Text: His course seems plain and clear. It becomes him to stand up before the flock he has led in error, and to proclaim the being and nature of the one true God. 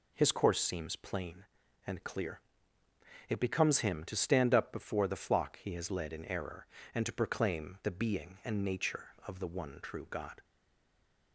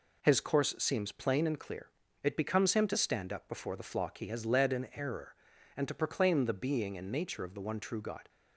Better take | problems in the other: second | stays silent after the last word; slight; from 10.4 s on; 0.9 s long

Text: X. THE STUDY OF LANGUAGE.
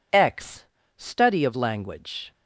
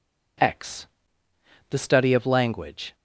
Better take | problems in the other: second | skips "THE"; at 0.8 s

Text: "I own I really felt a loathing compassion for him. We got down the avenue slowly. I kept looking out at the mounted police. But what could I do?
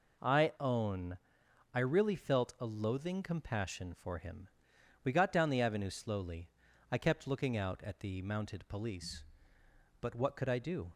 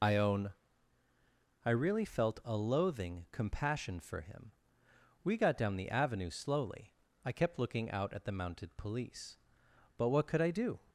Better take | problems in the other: first | loses the start of "I"; at 0.0 s; 45 ms // pauses between "own" and "I"; at 0.5 s; 1.1 s long; noticeable in the first

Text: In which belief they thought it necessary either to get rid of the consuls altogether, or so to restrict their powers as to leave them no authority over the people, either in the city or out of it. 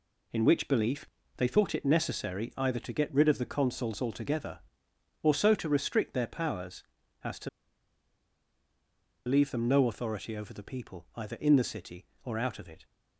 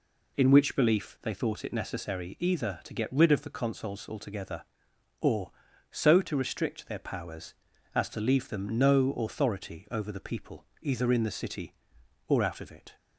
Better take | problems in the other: second | pauses between "belief" and "they"; slight; at 1.0 s; 0.32 s long // pauses between "to" and "leave"; strong; at 7.4 s; 1.7 s long

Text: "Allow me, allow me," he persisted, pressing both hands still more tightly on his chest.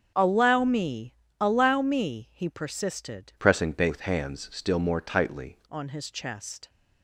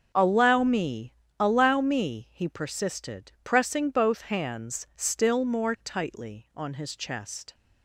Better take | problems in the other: second | starts louder than the rest; until 1.4 s; 6.5 dB; also in the second // changes voice from "pressing" to "tightly"; from 3.3 to 5.5 s; 2.2 s long

